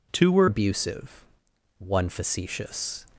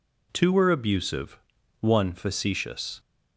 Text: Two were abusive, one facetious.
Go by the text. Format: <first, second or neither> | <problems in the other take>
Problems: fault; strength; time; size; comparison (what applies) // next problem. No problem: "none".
second | changes voice at "abusive"; from 0.4 s on; 2.6 s long